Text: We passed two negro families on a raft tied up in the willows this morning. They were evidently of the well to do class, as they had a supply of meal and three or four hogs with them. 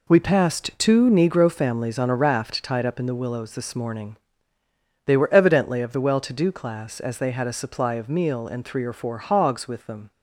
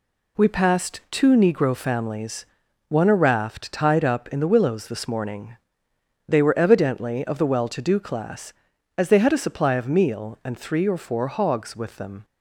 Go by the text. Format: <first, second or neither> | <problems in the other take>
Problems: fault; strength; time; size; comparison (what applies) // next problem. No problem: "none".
first | says "one" for "on"; at 2.8 s